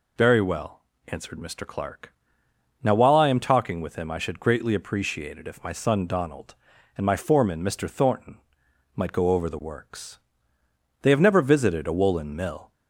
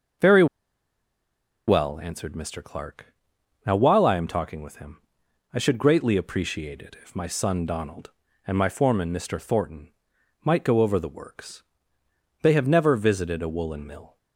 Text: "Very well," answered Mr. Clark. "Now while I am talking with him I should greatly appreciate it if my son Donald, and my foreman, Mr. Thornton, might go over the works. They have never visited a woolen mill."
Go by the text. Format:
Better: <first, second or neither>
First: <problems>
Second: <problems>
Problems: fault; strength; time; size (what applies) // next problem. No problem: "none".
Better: first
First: none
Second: starts louder than the rest; noticeable; until 2.4 s; 6 dB // pauses between "Very" and "well"; at 0.4 s; 1.2 s long // pauses between "him" and "I"; noticeable; at 5.0 s; 0.52 s long